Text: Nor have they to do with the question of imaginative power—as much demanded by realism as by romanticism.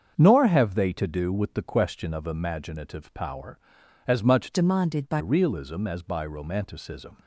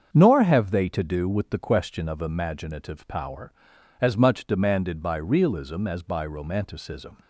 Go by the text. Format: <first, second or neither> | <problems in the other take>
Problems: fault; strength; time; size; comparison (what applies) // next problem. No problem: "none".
second | starts louder than the rest; until 1.1 s; 7 dB; also in the second // changes voice from "demanded" to "by"; from 4.5 to 5.2 s; 0.7 s long